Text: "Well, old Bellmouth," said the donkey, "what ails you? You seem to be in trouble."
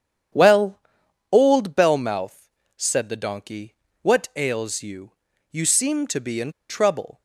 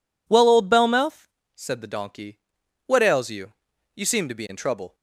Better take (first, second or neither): second